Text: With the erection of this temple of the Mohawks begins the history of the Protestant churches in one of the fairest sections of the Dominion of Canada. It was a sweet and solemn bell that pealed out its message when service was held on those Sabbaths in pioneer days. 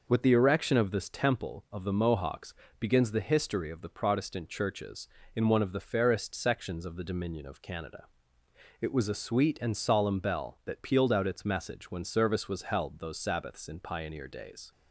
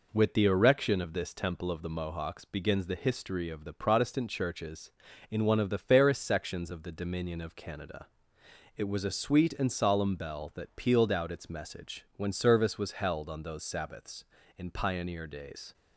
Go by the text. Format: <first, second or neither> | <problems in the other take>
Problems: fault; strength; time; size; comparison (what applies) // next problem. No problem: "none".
second | pauses between "Mohawks" and "begins"; slight; at 2.5 s; 0.26 s long // skips "on"; at 13.0 s